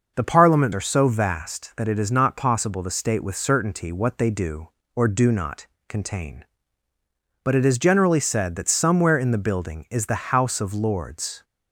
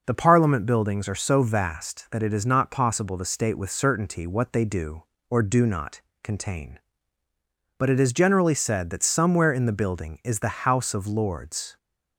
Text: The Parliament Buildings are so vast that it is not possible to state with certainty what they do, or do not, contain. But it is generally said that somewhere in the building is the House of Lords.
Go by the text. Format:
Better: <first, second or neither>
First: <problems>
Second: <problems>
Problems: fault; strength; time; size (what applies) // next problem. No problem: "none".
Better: second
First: skips "Buildings"; at 0.7 s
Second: none